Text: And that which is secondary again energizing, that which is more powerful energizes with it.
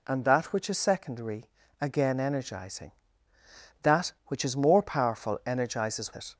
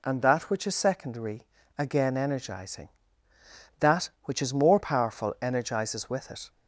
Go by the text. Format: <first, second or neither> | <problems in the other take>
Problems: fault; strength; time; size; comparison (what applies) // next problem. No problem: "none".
second | pauses between "secondary" and "again"; slight; at 1.4 s; 0.36 s long; slight in the second // skips "with"; at 6.1 s